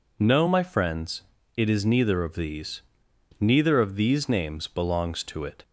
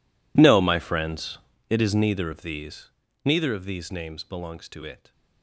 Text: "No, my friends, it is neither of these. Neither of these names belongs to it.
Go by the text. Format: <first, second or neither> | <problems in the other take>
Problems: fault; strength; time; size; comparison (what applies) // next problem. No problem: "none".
first | gets quieter; strong; throughout; 21.5 dB